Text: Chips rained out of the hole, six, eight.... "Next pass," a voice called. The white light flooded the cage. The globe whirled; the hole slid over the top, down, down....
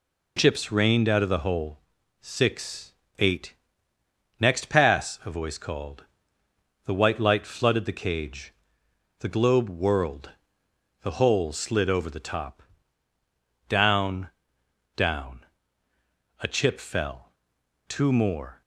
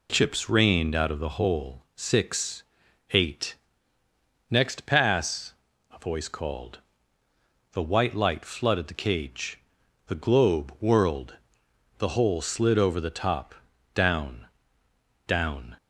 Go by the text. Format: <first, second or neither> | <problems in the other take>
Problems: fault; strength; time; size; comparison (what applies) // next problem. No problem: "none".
second | goes on to say "A chip fell two more"; strong; from 16.3 s on; 2.2 s long